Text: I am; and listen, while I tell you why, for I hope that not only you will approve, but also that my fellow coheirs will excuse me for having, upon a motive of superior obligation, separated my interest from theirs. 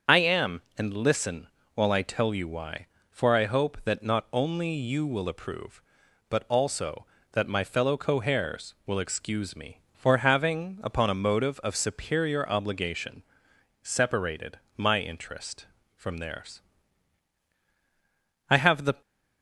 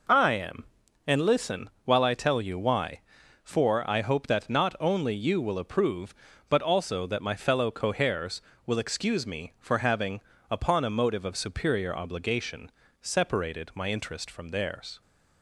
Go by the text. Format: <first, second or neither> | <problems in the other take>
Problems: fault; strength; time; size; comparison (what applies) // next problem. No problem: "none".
second | starts louder than the rest; until 1.2 s; 7 dB // pauses between "separated" and "my"; slight; at 14.5 s; 0.18 s long // goes on to say "I have the"; from 18.4 s on; 0.52 s long